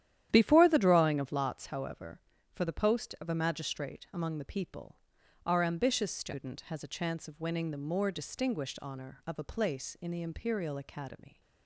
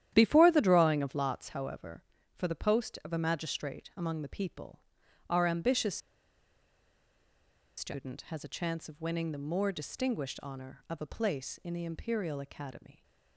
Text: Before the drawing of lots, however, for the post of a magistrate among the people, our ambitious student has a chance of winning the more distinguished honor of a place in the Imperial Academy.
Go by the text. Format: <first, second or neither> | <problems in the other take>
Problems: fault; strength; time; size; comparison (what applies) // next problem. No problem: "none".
first | starts louder than the rest; strong; until 1.1 s; 11 dB; strong in the first // pauses between "ambitious" and "student"; strong; at 5.9 s; 1.7 s long